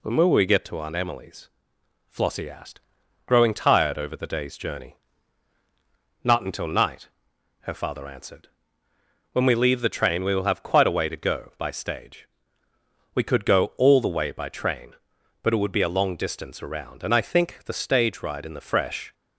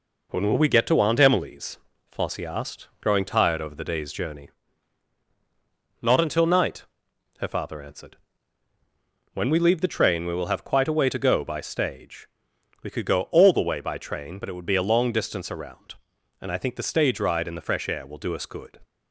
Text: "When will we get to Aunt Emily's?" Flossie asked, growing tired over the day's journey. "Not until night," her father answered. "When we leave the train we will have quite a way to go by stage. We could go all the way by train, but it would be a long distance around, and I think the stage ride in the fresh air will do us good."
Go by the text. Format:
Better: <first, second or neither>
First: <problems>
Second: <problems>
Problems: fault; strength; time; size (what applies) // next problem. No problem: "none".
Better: second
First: stops before "air will do us good"; at 19.1 s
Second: none